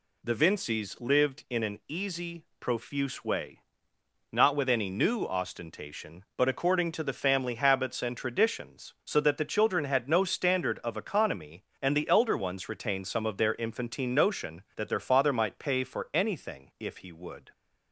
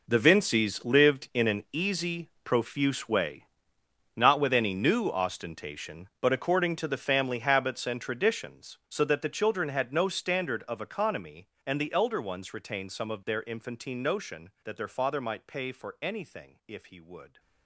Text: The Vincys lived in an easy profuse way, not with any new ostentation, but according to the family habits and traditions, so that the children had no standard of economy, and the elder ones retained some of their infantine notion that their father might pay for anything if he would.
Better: first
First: none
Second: gets quieter; strong; throughout; 14 dB

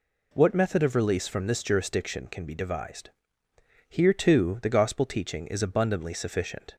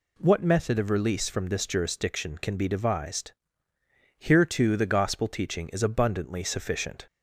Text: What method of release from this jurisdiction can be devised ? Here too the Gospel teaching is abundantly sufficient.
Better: neither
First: none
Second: none

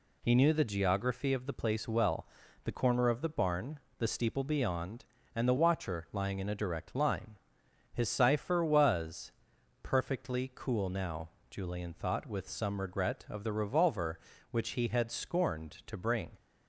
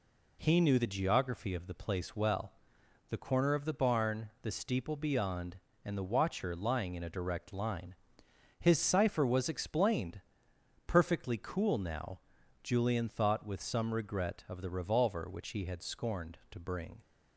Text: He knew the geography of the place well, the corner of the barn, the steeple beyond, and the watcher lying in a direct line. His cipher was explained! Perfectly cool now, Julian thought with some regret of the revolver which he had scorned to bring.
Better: second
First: skips "explained"; at 9.5 s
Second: none

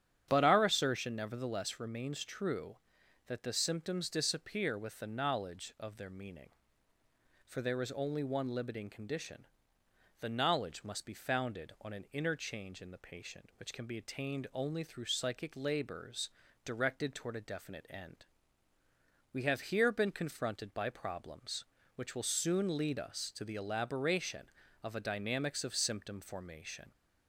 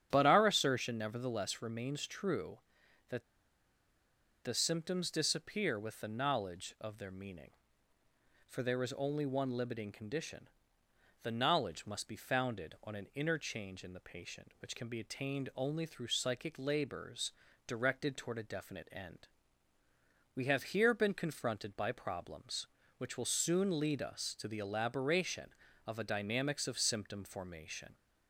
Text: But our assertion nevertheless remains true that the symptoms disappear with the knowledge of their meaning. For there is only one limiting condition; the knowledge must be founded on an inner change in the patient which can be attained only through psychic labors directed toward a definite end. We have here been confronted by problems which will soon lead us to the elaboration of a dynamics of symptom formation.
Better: first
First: starts louder than the rest; strong; until 1.3 s; 9 dB // pauses between "labors" and "directed"; at 16.2 s; 0.38 s long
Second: starts louder than the rest; strong; until 1.1 s; 9 dB // pauses between "that" and "the"; at 3.2 s; 1.1 s long // pauses between "labors" and "directed"; at 17.3 s; 0.38 s long

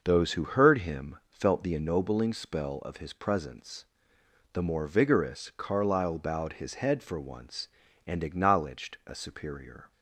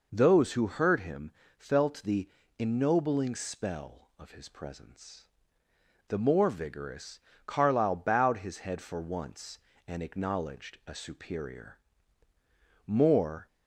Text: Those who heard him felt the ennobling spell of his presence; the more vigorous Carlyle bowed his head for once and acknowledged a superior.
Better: first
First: none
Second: pauses between "him" and "felt"; slight; at 1.3 s; 0.26 s long // pauses between "the" and "ennobling"; slight; at 2.2 s; 0.30 s long // pauses between "vigorous" and "Carlyle"; slight; at 7.2 s; 0.26 s long // goes on to say "More"; noticeable; from 12.8 s on; 0.62 s long

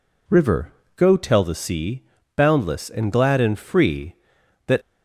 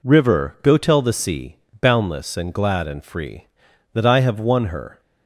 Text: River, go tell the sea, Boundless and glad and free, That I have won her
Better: second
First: stops before "I have won her"; at 4.8 s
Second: none

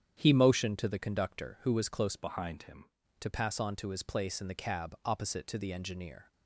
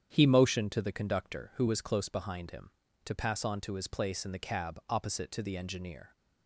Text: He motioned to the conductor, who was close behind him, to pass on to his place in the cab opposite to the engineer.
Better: second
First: starts louder than the rest; strong; until 1.2 s; 8.5 dB // changes voice from "behind" to "him"; from 2.1 to 2.8 s; 0.7 s long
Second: starts louder than the rest; strong; until 1.1 s; 9 dB

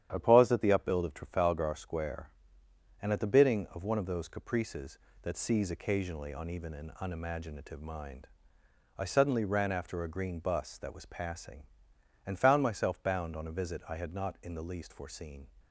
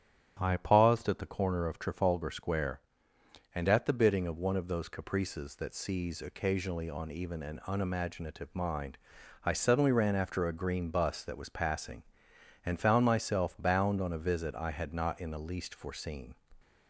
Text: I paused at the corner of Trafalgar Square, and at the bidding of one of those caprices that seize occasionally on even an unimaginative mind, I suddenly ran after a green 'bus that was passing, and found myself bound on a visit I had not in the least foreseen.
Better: second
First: starts louder than the rest; strong; until 1.1 s; 10 dB // says "upbuild" for "corner"; at 0.7 s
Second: starts louder than the rest; strong; until 1.4 s; 10 dB

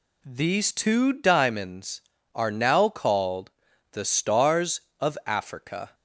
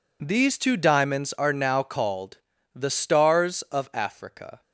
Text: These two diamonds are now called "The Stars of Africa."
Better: neither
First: pauses between "called" and "The"; at 3.4 s; 0.40 s long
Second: pauses between "called" and "The"; at 2.3 s; 0.38 s long

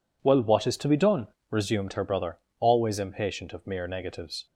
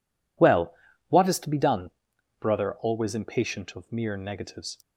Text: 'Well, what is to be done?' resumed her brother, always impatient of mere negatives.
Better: first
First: none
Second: skips "resumed her"; at 2.1 s

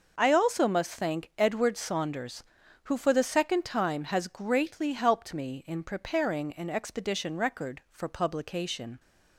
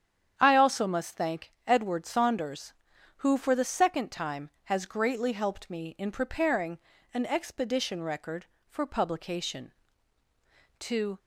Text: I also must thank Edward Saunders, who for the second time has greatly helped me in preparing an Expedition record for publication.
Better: first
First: none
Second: starts louder than the rest; strong; until 1.3 s; 9 dB // pauses between "thank" and "Edward"; slight; at 1.5 s; 0.16 s long // pauses between "preparing" and "an"; slight; at 6.7 s; 0.36 s long // goes on to say "To"; slight; from 10.8 s on; 0.38 s long

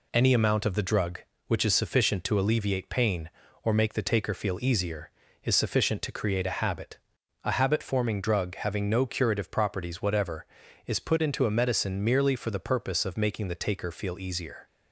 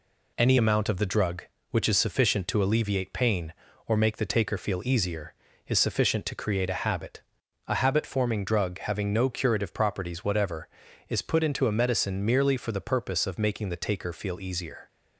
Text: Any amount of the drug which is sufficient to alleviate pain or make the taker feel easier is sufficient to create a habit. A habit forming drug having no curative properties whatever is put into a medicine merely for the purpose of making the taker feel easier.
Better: neither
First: none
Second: none

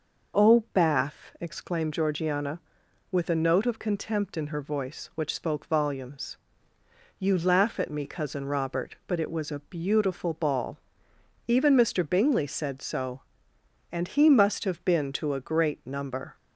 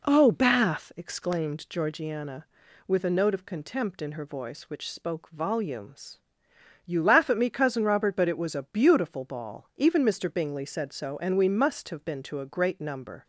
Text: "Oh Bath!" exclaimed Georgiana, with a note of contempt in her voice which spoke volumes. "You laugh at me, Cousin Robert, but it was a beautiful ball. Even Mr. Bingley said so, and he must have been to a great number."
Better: first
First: none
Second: says "we" for "he"; at 11.3 s

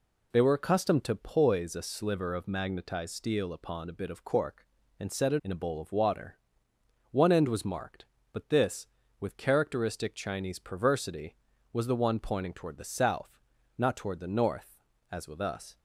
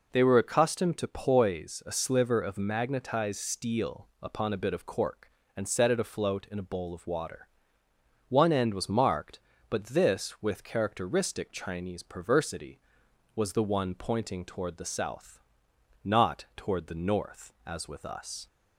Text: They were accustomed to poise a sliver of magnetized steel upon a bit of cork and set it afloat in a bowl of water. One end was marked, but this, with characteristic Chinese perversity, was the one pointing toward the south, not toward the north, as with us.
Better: second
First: skips "afloat"; at 5.4 s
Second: none

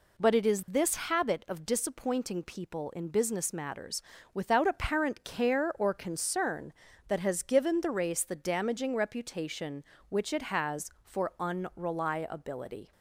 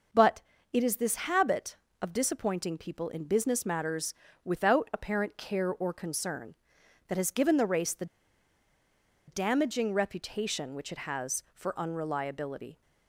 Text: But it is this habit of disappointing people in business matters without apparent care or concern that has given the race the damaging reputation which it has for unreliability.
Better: first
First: pauses between "matters" and "without"; slight; at 4.0 s; 0.32 s long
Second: pauses between "But" and "it"; slight; at 0.4 s; 0.32 s long // pauses between "matters" and "without"; slight; at 4.1 s; 0.30 s long // pauses between "the" and "damaging"; at 8.0 s; 1.2 s long

